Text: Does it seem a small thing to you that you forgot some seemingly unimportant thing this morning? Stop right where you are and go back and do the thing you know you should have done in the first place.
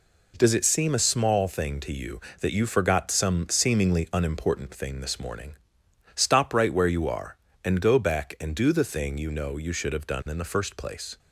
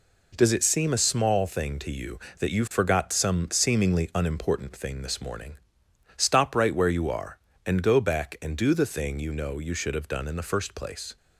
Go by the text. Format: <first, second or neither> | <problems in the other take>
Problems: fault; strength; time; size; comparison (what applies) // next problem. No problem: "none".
neither | none